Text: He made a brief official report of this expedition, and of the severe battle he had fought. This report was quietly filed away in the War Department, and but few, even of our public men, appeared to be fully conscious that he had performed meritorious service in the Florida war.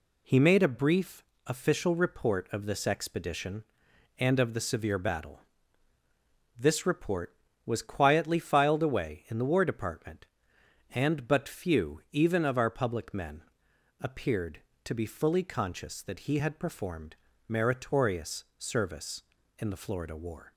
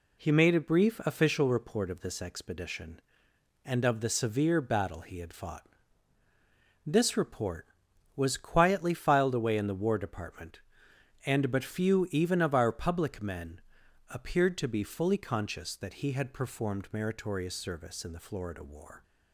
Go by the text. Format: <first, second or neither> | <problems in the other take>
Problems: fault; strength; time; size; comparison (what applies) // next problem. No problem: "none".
second | pauses between "brief" and "official"; slight; at 1.2 s; 0.22 s long // skips "he had fought"; at 5.9 s // pauses between "performed" and "meritorious"; slight; at 17.1 s; 0.32 s long